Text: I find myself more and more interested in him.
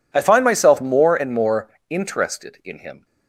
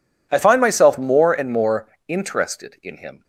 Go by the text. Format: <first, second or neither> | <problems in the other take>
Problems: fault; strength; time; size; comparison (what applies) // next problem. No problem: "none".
neither | pauses between "more" and "interested"; slight; the same in both